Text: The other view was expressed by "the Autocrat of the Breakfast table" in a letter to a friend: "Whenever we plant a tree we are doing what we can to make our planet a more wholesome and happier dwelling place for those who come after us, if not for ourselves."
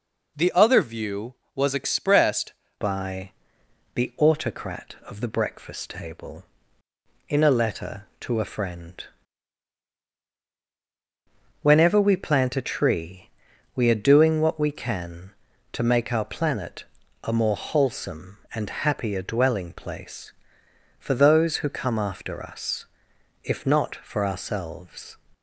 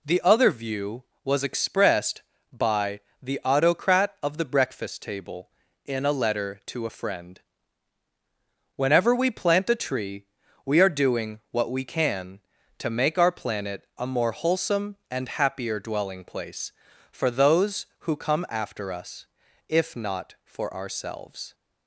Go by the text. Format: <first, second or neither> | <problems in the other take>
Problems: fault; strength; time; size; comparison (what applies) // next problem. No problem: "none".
second | changes voice at "by"; from 2.8 s on; 22.3 s long // pauses between "by" and "the"; noticeable; at 3.3 s; 0.62 s long; slight in the second // pauses between "tree" and "we"; noticeable; at 13.2 s; 0.46 s long; also in the second // pauses between "planet" and "a"; at 16.8 s; 0.40 s long